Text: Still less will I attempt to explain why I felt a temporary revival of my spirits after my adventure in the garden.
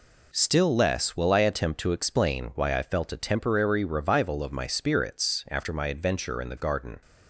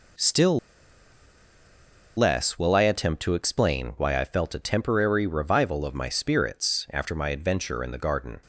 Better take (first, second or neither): first